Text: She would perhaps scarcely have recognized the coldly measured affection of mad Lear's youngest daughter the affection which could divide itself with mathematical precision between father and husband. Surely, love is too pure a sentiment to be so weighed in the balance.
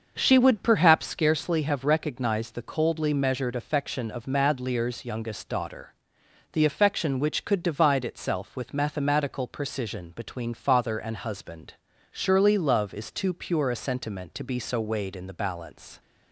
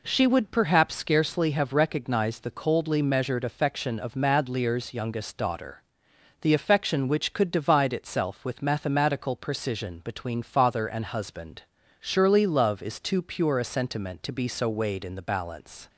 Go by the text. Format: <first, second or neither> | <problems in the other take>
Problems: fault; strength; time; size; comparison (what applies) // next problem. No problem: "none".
second | starts louder than the rest; until 1.1 s; 6.5 dB // pauses between "daughter" and "the"; noticeable; at 5.9 s; 0.60 s long; noticeable in the second